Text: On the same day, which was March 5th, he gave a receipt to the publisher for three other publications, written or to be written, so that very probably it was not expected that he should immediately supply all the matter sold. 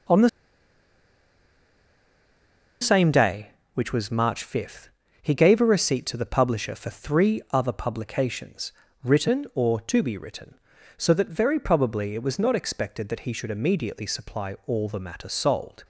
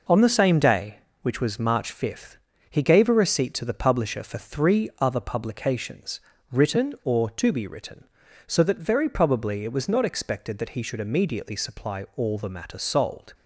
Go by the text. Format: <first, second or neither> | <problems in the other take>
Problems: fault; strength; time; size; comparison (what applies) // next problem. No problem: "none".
second | pauses between "the" and "same"; strong; at 0.2 s; 2.5 s long